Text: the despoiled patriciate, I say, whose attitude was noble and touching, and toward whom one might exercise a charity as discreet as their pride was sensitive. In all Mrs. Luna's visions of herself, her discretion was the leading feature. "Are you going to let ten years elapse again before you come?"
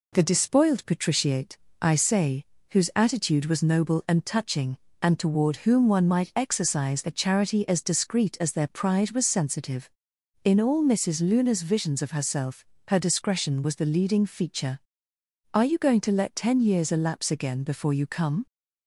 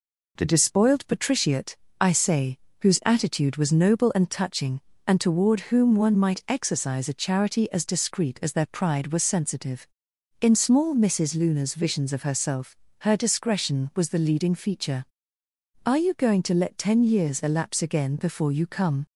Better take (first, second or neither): first